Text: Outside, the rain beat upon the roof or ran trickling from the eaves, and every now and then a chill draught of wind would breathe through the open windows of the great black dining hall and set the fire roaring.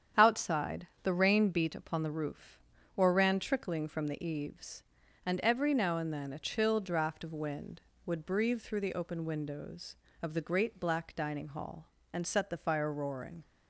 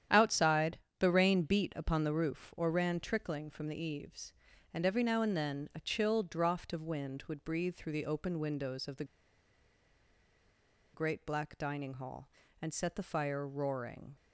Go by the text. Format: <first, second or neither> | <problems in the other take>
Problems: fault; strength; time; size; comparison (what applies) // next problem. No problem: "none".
first | starts louder than the rest; strong; until 1.3 s; 10 dB; strong in the first // pauses between "the" and "great"; strong; at 9.0 s; 1.8 s long